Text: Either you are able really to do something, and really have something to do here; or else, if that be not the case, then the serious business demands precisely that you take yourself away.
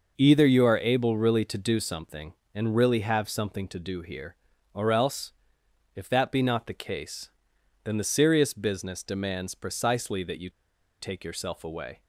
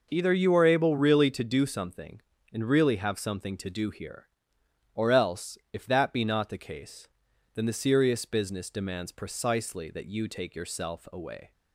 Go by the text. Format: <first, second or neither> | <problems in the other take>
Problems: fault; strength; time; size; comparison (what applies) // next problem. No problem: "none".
second | pauses between "you" and "take"; noticeable; at 10.4 s; 0.49 s long